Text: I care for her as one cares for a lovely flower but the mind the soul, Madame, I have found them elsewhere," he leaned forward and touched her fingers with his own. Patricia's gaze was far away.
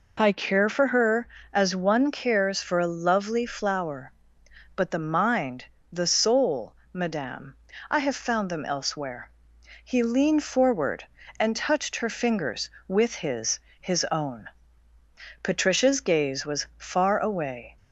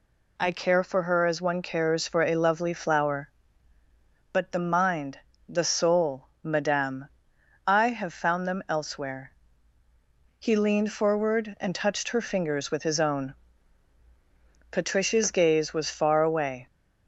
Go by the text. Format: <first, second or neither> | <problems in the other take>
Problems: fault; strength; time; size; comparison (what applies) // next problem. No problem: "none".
second | pauses between "mind" and "the"; slight; at 5.6 s; 0.28 s long; slight in the second // says "his" twice; at 13.8 s